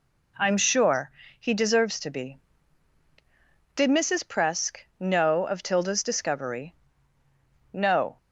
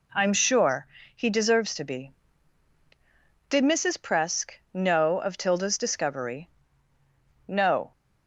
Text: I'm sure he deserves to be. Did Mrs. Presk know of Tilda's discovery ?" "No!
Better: neither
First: pauses between "sure" and "he"; slight; at 1.1 s; 0.26 s long // pauses between "Presk" and "know"; slight; at 4.7 s; 0.20 s long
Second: pauses between "sure" and "he"; slight; at 0.8 s; 0.26 s long // pauses between "Presk" and "know"; slight; at 4.5 s; 0.20 s long

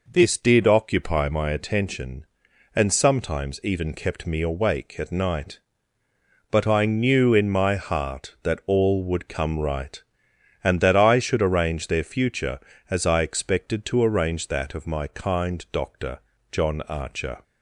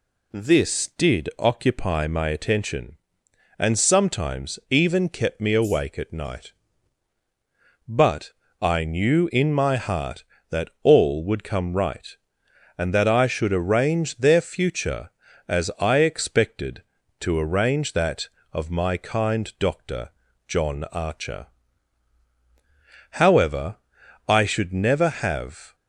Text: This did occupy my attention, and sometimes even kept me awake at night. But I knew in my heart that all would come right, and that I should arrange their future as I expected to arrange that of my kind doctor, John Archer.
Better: first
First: none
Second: pauses between "But" and "I"; slight; at 8.3 s; 0.30 s long // goes on to say "However I should never have"; strong; from 23.1 s on; 2.6 s long

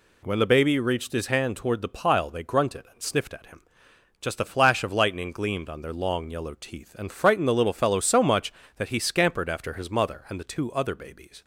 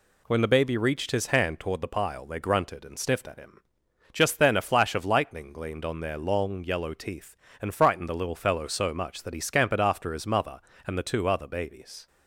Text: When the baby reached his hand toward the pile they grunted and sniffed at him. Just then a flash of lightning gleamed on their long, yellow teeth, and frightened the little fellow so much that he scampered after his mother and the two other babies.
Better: second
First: skips "then"; at 4.3 s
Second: none

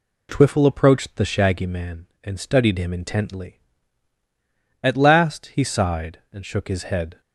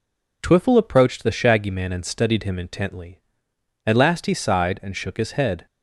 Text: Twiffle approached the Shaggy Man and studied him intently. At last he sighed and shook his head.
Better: neither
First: none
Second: none

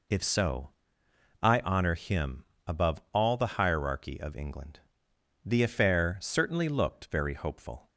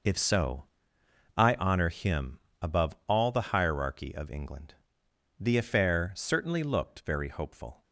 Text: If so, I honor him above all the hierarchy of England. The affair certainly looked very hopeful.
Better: first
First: pauses between "him" and "above"; slight; at 2.4 s; 0.22 s long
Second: gets quieter; strong; throughout; 11 dB // pauses between "him" and "above"; slight; at 2.3 s; 0.22 s long

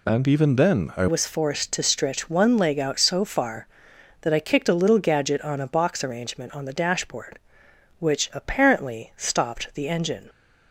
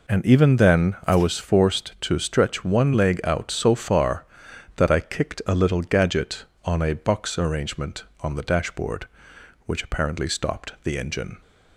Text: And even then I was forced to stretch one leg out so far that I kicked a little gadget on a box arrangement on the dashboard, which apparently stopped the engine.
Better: second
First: changes voice at "was"; from 1.0 s on; 9.2 s long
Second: none

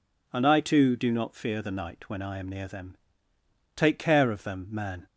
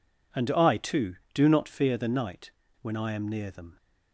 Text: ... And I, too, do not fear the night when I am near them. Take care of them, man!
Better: first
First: none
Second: pauses between "night" and "when"; slight; at 2.5 s; 0.28 s long // stops before "Take care of them man"; at 3.7 s

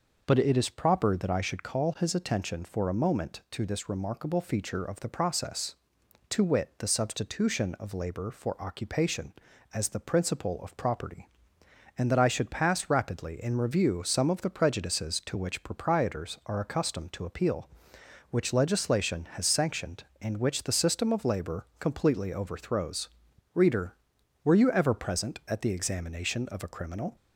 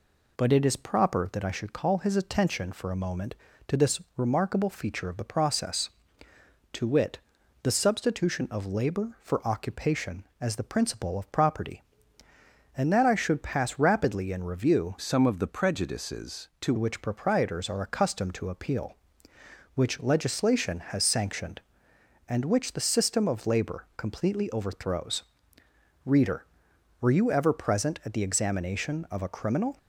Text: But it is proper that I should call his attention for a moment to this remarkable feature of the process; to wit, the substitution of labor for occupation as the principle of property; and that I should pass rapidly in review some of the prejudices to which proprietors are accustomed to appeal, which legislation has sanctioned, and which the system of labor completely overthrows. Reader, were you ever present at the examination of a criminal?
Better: first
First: none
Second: pauses between "this" and "remarkable"; slight; at 4.0 s; 0.16 s long // changes voice from "some" to "to"; from 14.9 to 16.7 s; 1.8 s long

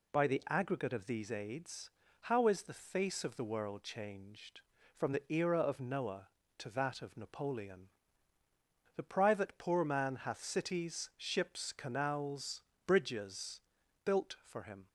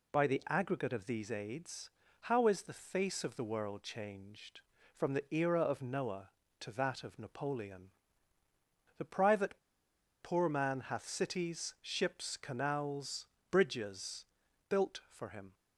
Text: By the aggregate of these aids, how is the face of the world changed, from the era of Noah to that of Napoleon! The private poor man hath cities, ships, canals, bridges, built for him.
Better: first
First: none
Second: pauses between "private" and "poor"; noticeable; at 9.5 s; 0.63 s long

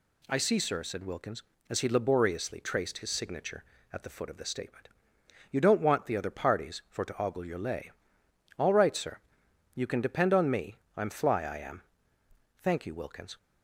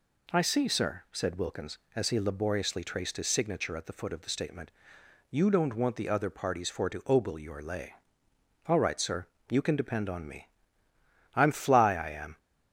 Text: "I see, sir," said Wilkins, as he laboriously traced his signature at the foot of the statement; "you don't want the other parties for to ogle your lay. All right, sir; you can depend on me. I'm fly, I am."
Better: second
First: goes on to say "Thank you Wilkins"; noticeable; from 12.5 s on; 0.80 s long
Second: none

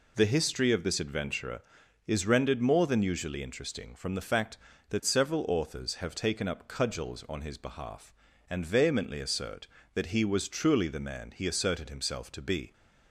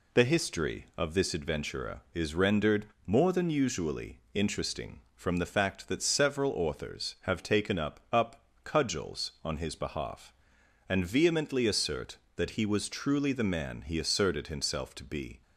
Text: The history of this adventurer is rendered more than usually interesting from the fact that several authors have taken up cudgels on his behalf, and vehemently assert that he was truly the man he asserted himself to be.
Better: first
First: none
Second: pauses between "rendered" and "more"; slight; at 2.8 s; 0.20 s long // pauses between "usually" and "interesting"; slight; at 4.1 s; 0.16 s long // says "up" twice; at 8.1 s

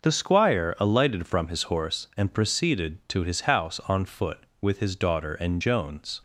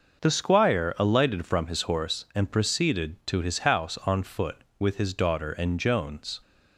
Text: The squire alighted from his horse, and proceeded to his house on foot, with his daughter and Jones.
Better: neither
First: none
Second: none

